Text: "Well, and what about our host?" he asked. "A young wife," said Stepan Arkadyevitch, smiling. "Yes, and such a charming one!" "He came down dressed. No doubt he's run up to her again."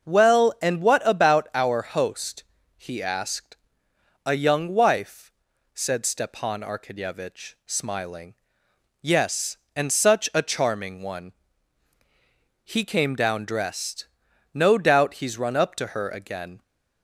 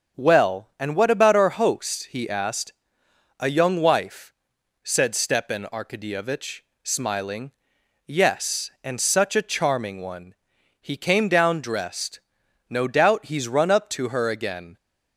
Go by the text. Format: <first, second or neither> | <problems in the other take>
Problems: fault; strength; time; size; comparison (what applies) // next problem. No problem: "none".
neither | starts louder than the rest; the same in both